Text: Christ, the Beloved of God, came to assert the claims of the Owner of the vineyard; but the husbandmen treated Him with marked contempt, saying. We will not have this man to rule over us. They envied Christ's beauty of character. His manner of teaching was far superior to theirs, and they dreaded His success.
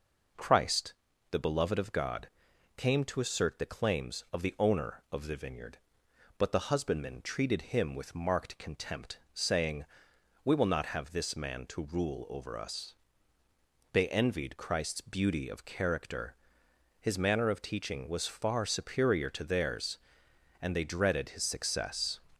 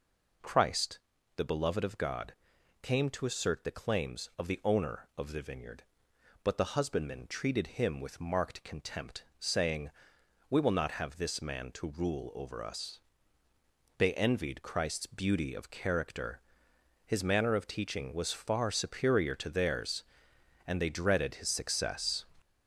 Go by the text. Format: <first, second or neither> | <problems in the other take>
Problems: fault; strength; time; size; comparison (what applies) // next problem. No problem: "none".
first | gets louder; noticeable; throughout; 5 dB